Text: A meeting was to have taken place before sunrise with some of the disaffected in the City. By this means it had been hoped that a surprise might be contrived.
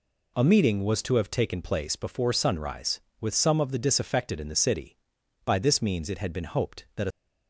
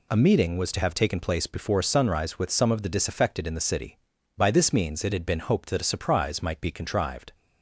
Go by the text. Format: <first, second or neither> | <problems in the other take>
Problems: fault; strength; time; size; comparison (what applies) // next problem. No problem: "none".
second | stops before "surprise might be contrived"; at 7.1 s